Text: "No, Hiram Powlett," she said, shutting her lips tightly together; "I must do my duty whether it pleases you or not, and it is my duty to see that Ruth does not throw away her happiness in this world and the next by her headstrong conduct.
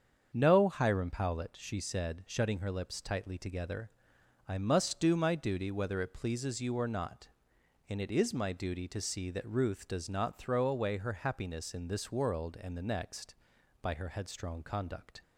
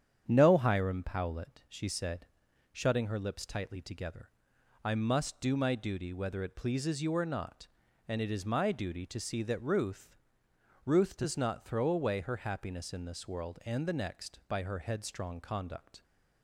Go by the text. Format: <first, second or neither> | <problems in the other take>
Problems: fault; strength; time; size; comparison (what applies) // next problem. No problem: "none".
first | starts louder than the rest; strong; until 1.2 s; 8.5 dB; strong in the first // says "Ruth" twice; at 10.8 s